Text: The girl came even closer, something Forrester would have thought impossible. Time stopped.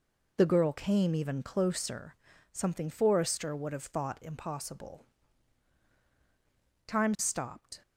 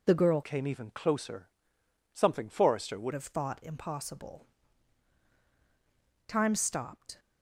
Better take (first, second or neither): first